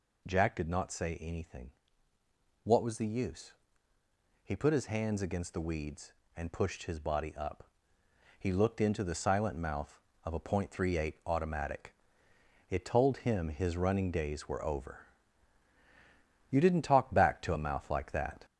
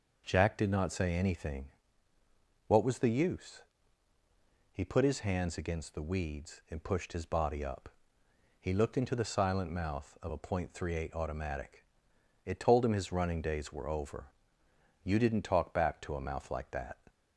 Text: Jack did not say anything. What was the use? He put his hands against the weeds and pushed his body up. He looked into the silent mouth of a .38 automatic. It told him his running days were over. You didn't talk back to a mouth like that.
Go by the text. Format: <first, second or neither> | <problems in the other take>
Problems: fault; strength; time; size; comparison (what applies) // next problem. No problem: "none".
second | gets louder; noticeable; throughout; 4.5 dB